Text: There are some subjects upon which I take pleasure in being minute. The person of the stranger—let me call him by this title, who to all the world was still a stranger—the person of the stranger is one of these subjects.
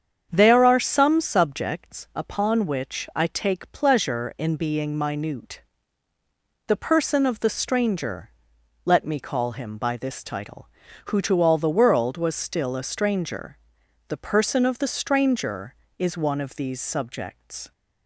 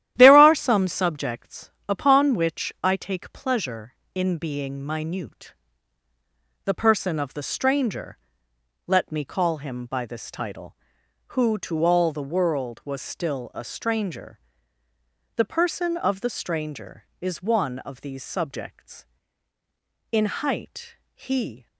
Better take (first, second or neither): first